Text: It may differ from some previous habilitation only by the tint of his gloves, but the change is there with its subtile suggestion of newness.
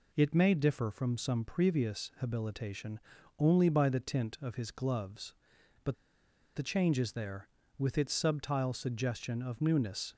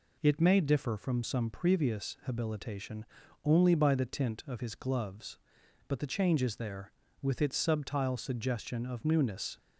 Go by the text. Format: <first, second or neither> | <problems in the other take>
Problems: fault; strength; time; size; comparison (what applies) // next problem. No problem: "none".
second | pauses between "habilitation" and "only"; at 2.9 s; 0.38 s long; also in the second // pauses between "but" and "the"; noticeable; at 5.9 s; 0.60 s long